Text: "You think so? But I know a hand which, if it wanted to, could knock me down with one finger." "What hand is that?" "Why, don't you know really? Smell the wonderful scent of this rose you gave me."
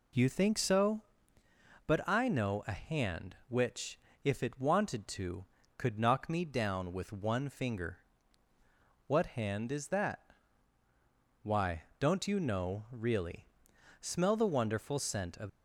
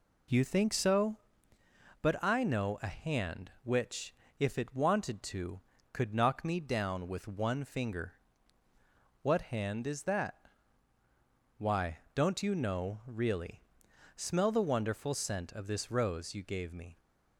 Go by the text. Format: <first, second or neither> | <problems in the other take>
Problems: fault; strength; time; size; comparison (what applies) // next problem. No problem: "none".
second | stops before "this rose you gave me"; at 15.4 s